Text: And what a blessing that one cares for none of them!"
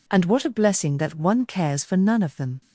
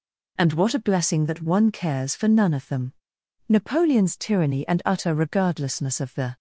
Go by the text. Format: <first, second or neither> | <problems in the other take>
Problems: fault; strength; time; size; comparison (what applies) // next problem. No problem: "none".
first | goes on to say "Napoleon's tyranny and utter regardlessness of the"; strong; from 3.4 s on; 2.8 s long